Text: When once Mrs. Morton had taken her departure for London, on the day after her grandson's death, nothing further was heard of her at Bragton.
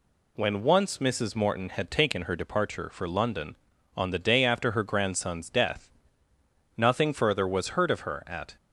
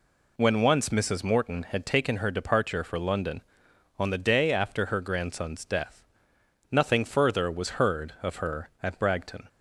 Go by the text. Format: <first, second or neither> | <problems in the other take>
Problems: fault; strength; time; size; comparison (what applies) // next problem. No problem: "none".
second | stops before "Bragton"; at 8.5 s